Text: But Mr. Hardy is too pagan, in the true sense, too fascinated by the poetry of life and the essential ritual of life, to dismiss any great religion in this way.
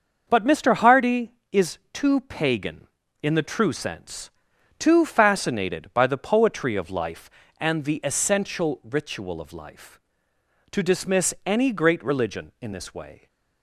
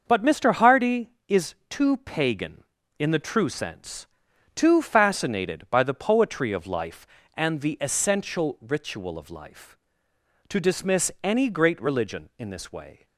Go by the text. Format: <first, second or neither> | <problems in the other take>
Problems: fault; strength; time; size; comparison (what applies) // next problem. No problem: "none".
neither | starts louder than the rest; the same in both // pauses between "is" and "too"; slight; the same in both